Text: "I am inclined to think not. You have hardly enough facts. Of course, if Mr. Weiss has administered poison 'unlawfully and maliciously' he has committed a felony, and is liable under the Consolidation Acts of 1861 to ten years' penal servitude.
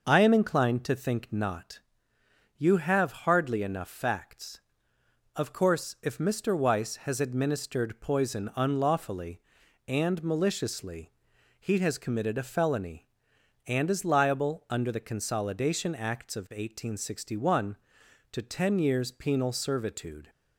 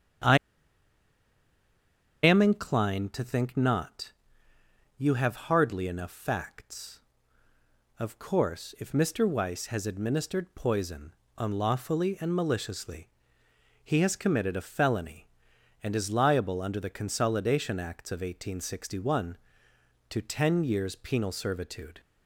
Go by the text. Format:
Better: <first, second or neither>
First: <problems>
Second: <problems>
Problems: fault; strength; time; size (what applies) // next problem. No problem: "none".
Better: first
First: pauses between "maliciously" and "he"; noticeable; at 11.1 s; 0.48 s long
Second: starts louder than the rest; strong; until 3.0 s; 8.5 dB // pauses between "I" and "am"; strong; at 0.3 s; 1.8 s long // pauses between "poison" and "unlawfully"; slight; at 11.1 s; 0.24 s long // pauses between "maliciously" and "he"; noticeable; at 13.1 s; 0.74 s long